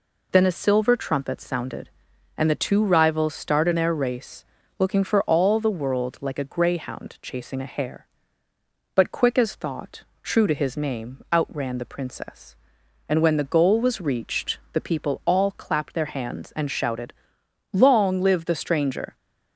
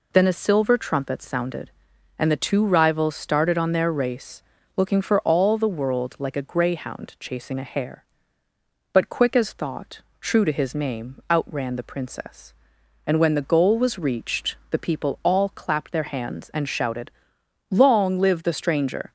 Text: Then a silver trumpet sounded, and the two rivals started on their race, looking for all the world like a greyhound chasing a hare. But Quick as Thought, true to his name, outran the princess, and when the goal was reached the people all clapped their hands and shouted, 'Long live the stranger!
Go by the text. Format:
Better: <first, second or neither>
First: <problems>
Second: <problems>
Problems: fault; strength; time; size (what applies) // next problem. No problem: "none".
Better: second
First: skips "on"; at 3.7 s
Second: none